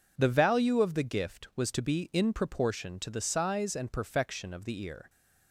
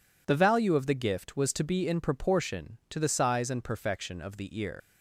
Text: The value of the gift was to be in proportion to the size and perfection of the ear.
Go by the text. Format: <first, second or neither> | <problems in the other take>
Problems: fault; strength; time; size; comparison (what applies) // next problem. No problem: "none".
first | leaves "ear" unfinished; at 4.8 s; 85 ms